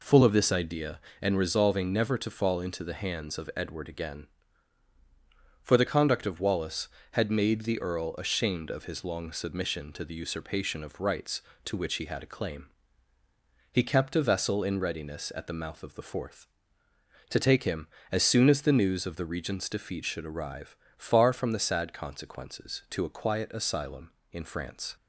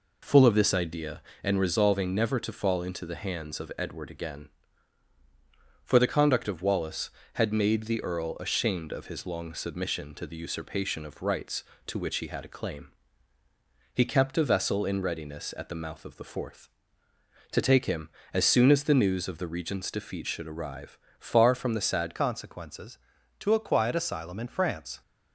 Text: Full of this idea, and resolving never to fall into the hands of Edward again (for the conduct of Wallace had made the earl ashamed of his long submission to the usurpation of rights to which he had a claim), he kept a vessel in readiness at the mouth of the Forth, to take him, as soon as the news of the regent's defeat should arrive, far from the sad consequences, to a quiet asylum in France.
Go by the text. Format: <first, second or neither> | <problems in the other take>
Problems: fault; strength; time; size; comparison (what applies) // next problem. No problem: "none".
first | changes voice at "consequences"; from 22.1 s on; 2.9 s long